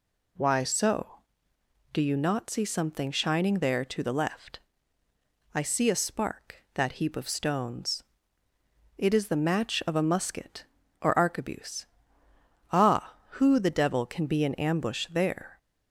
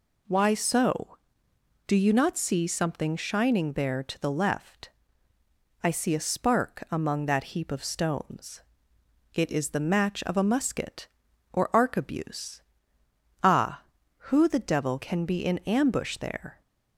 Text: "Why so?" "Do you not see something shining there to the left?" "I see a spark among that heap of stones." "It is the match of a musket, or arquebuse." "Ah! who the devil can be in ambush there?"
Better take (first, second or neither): second